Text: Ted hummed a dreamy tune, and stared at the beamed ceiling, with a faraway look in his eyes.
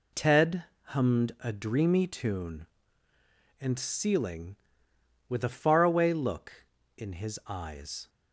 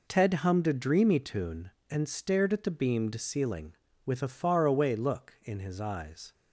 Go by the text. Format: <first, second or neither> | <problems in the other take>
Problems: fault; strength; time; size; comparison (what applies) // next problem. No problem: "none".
second | pauses between "Ted" and "hummed"; slight; at 0.6 s; 0.22 s long // skips "stared at the beamed"; at 3.7 s